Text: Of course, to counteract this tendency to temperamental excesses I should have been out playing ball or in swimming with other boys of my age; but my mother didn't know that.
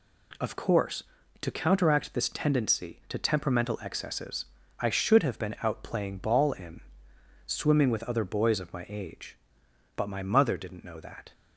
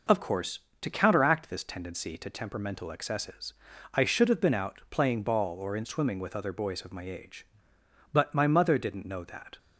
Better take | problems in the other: second | pauses between "excesses" and "I"; slight; at 4.4 s; 0.34 s long; also in the second // skips "or"; at 6.5 s // pauses between "in" and "swimming"; noticeable; at 6.7 s; 0.66 s long

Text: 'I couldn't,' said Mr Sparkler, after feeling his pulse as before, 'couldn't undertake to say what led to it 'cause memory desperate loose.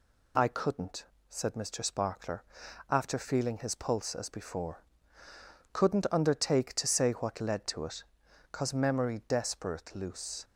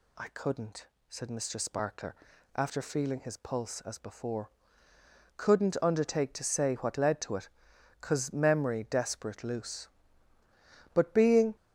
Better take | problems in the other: first | pauses between "it" and "cause"; noticeable; at 7.4 s; 0.50 s long; noticeable in the first // goes on to say "But being"; noticeable; from 10.9 s on; 0.62 s long

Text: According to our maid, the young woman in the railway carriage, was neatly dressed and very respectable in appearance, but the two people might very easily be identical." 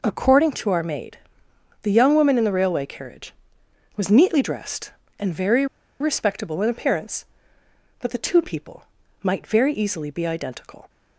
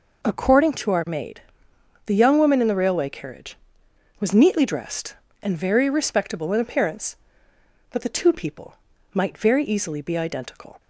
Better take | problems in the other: second | pauses between "very" and "respectable"; slight; at 5.6 s; 0.33 s long // pauses between "people" and "might"; slight; at 8.8 s; 0.36 s long; slight in the second

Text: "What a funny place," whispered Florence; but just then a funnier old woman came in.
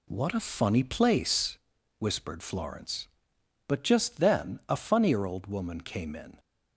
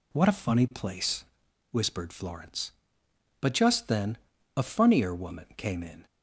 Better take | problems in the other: first | pauses between "then" and "a"; at 4.1 s; 0.40 s long // skips "old"; at 5.1 s

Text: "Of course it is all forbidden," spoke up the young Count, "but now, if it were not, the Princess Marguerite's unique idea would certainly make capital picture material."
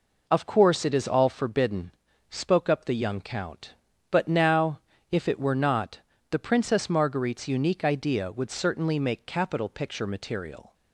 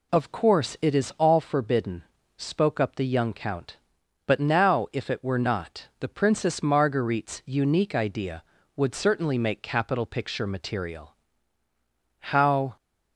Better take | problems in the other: first | goes on to say "How"; from 12.1 s on; 0.56 s long

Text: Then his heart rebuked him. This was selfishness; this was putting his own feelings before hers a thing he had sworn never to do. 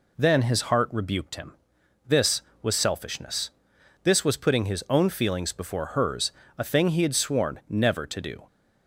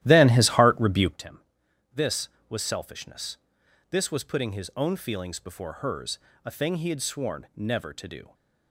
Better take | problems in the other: first | starts louder than the rest; strong; until 1.2 s; 14 dB // pauses between "hers" and "a"; slight; at 6.1 s; 0.26 s long; slight in the first

